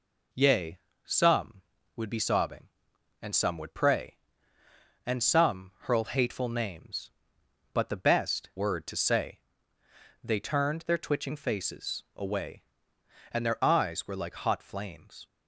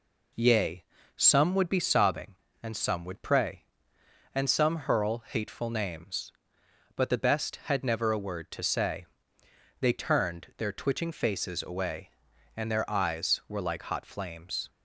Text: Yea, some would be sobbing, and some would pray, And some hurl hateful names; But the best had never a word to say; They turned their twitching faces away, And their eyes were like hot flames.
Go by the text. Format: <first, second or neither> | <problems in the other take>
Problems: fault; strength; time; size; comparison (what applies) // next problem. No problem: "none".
second | skips "had never a"; at 8.5 s